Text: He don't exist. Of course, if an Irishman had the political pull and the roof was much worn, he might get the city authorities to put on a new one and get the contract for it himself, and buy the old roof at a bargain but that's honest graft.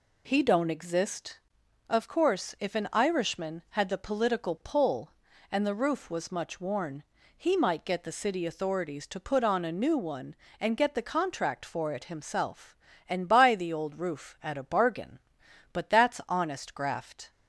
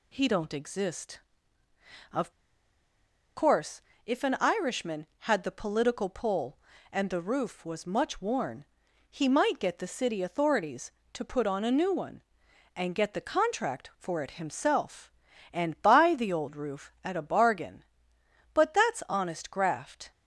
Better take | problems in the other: first | pauses between "Of" and "course"; at 2.3 s; 1.0 s long

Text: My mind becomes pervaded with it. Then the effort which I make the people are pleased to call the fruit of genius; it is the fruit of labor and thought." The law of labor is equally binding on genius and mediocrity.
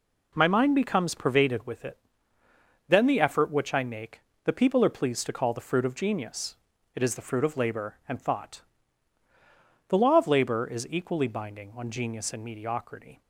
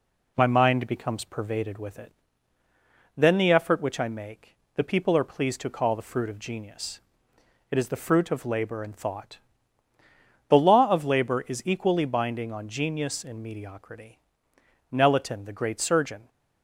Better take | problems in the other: first | pauses between "make" and "the"; slight; at 4.5 s; 0.20 s long; slight in the first // goes on to say "Nelaton the great surgeon"; from 14.9 s on; 1.3 s long

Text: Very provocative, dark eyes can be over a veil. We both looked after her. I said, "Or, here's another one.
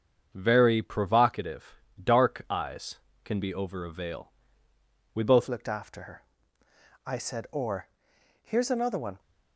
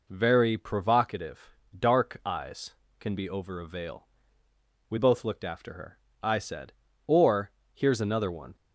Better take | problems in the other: second | starts louder than the rest; strong; until 1.3 s; 7.5 dB // changes voice at "looked"; from 5.4 s on; 3.7 s long

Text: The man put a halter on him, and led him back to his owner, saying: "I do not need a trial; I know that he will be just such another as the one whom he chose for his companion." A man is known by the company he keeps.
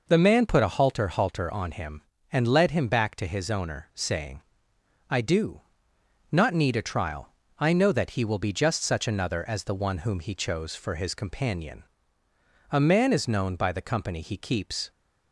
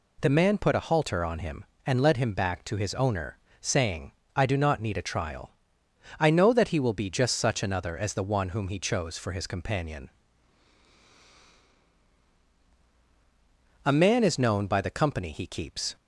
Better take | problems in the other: second | says "halter" twice; at 1.0 s // pauses between "do" and "not"; noticeable; at 5.6 s; 0.68 s long

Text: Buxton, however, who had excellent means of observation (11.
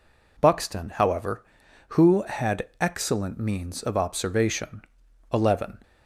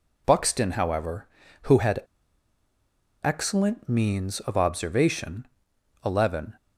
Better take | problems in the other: first | pauses between "had" and "excellent"; at 2.0 s; 1.2 s long

